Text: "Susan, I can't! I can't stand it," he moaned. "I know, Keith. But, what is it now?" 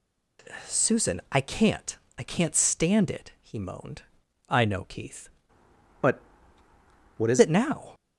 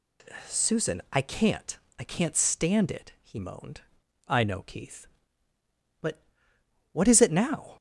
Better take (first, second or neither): second